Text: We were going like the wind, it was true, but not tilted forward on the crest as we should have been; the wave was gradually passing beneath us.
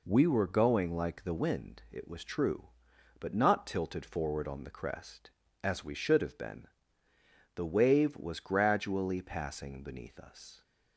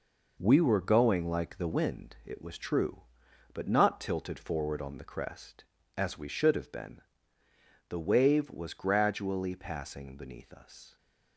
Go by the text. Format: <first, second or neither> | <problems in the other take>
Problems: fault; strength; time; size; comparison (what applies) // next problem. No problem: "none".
first | gets quieter; strong; throughout; 7.5 dB